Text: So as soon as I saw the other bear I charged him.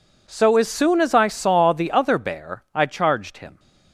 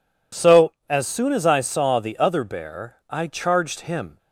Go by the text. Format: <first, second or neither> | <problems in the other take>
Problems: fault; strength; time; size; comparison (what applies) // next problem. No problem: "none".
neither | none